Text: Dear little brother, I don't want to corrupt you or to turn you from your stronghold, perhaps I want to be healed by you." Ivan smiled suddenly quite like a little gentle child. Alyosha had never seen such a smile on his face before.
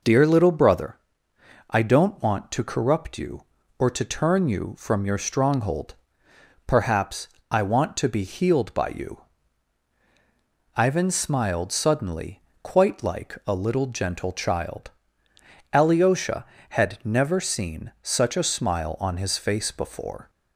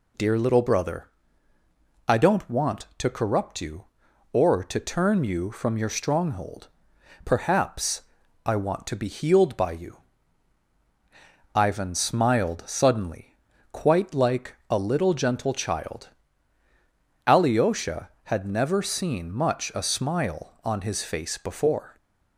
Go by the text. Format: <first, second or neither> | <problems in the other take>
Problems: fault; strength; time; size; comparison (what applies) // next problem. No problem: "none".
first | pauses between "perhaps" and "I"; at 8.0 s; 0.44 s long; slight in the first // pauses between "suddenly" and "quite"; at 13.3 s; 0.38 s long; slight in the first // pauses between "like" and "a"; slight; at 14.5 s; 0.16 s long // says "much" for "such"; at 19.3 s